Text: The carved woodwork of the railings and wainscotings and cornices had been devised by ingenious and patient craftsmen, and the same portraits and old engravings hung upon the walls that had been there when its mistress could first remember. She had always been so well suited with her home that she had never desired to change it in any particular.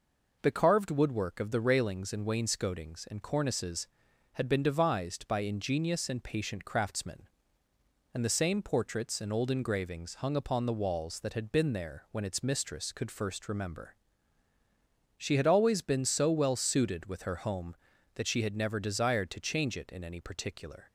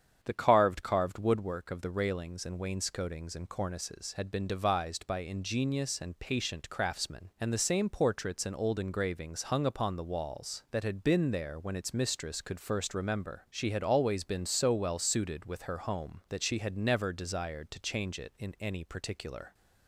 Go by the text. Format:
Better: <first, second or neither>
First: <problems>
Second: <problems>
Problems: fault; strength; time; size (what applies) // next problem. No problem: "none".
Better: first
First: none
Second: starts louder than the rest; strong; until 1.2 s; 8 dB // says "carved" twice; at 0.8 s